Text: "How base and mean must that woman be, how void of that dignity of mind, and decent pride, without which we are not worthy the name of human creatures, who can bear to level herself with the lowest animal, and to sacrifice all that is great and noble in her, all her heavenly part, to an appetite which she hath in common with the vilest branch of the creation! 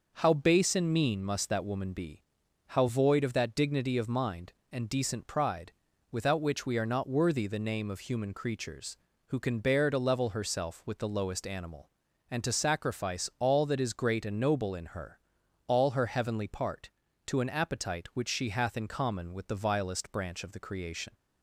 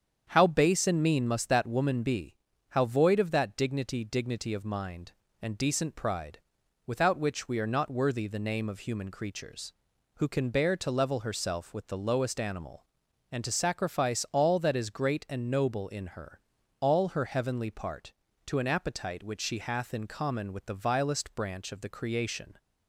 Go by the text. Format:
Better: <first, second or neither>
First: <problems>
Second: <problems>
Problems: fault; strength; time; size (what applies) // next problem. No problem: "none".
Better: first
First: none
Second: starts louder than the rest; strong; until 1.3 s; 8 dB // says "dignity" twice; at 4.0 s